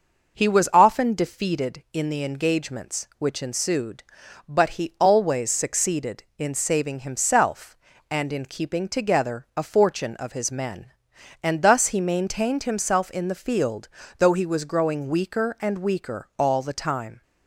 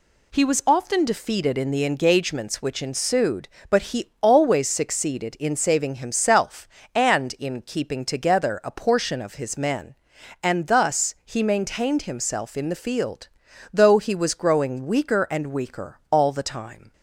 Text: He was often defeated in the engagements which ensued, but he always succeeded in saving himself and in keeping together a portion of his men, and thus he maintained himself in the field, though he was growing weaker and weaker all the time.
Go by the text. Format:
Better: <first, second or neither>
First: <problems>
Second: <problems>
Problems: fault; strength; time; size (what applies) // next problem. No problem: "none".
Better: second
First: says "fortune" for "portion"; at 9.6 s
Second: none